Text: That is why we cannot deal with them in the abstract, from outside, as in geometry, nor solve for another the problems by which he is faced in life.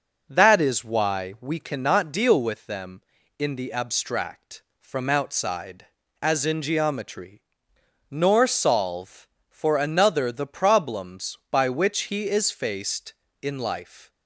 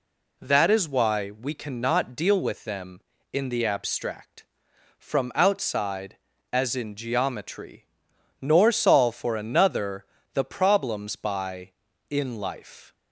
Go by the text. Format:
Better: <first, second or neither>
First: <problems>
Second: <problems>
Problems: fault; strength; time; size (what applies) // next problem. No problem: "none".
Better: first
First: none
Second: pauses between "another" and "the"; slight; at 10.0 s; 0.30 s long // skips "which he is faced"; at 11.9 s